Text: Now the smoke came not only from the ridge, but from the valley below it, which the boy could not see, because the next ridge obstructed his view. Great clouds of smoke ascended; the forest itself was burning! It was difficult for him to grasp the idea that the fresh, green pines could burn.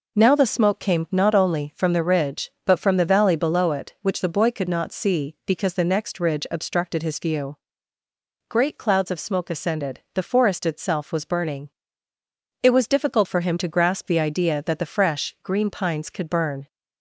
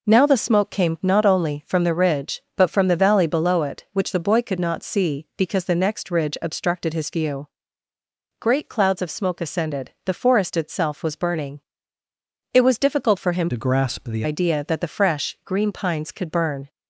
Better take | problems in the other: first | changes voice from "to" to "the"; from 13.4 to 14.2 s; 0.8 s long

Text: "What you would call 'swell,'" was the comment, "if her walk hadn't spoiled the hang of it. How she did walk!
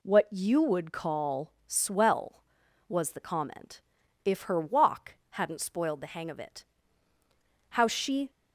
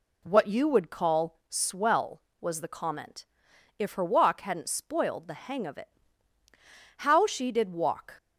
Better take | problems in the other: second | pauses between "call" and "swell"; slight; at 1.5 s; 0.16 s long // pauses between "walk" and "hadn't"; slight; at 5.1 s; 0.15 s long // stops before "did walk"; at 8.2 s

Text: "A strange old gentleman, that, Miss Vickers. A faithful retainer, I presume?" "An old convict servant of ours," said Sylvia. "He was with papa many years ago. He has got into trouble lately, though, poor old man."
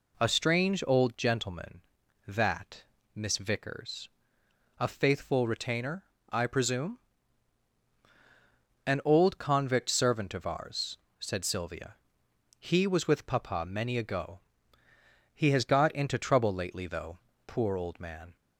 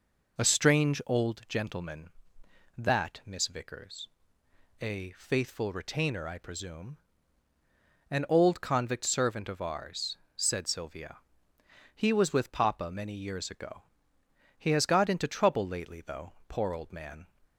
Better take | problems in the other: second | skips "years"; at 13.9 s

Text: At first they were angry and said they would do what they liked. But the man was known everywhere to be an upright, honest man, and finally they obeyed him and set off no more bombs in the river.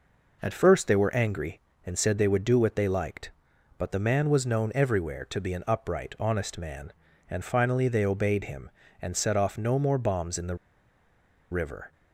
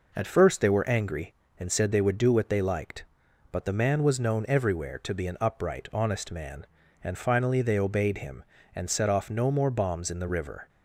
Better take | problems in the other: second | pauses between "the" and "river"; noticeable; at 10.5 s; 0.95 s long

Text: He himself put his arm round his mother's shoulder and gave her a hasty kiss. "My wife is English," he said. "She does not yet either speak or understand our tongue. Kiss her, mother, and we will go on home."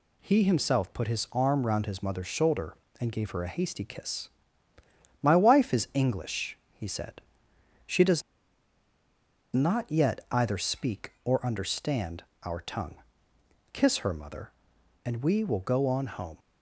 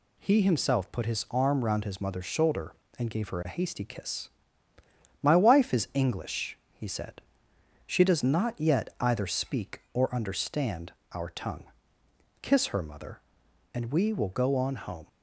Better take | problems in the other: second | pauses between "does" and "not"; strong; at 8.2 s; 1.3 s long // pauses between "understand" and "our"; slight; at 12.2 s; 0.22 s long; slight in the second

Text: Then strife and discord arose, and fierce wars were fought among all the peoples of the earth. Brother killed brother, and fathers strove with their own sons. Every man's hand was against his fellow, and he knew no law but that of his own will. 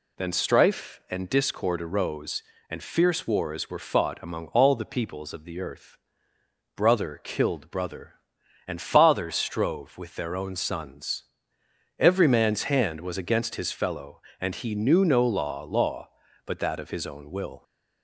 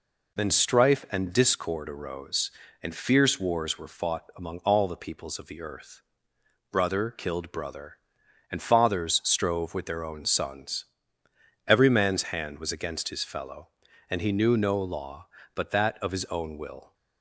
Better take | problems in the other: second | says "law" twice; at 15.6 s

